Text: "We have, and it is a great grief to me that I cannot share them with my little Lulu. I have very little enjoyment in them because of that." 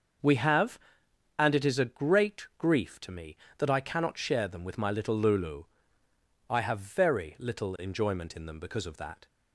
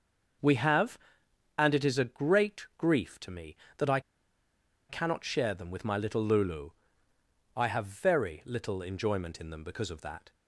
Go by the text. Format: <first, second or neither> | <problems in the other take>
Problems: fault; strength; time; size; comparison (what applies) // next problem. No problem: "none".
first | starts louder than the rest; until 2.0 s; 6.5 dB; also in the first // pauses between "I" and "cannot"; noticeable; at 3.9 s; 0.89 s long